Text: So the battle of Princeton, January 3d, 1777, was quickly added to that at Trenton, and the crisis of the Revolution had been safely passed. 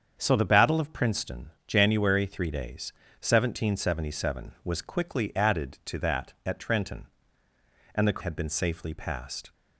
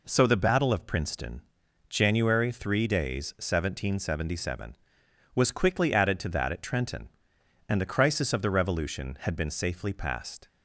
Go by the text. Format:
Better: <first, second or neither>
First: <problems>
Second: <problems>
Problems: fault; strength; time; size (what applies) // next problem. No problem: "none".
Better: second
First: starts louder than the rest; strong; until 1.2 s; 7.5 dB // skips "crisis of the Revolution"; at 8.1 s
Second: none